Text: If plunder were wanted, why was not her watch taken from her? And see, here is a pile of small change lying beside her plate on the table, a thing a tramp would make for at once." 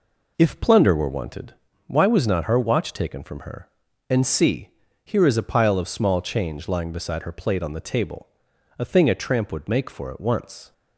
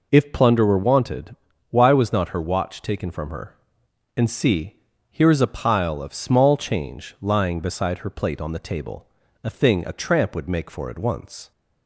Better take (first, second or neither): neither